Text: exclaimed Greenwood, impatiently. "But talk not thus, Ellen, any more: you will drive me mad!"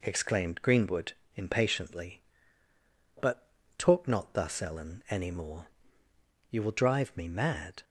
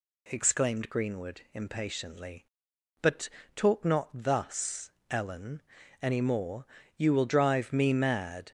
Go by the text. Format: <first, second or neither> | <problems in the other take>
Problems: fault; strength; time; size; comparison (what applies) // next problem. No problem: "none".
neither | pauses between "But" and "talk"; slight; the same in both